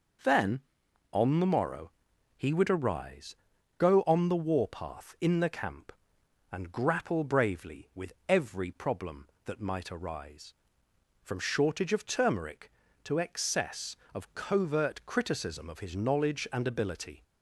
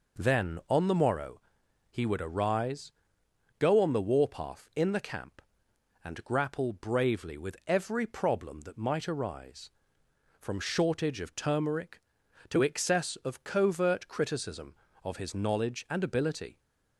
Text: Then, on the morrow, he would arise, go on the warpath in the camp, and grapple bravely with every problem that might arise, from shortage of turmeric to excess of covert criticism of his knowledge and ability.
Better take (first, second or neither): neither